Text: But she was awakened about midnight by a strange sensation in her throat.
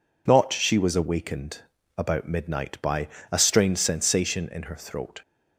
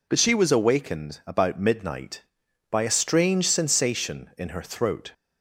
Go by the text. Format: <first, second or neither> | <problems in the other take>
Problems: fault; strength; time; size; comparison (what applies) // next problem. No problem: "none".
second | says "Not" for "But"; at 0.2 s // pauses between "awakened" and "about"; at 1.5 s; 0.38 s long // pauses between "by" and "a"; slight; at 3.0 s; 0.24 s long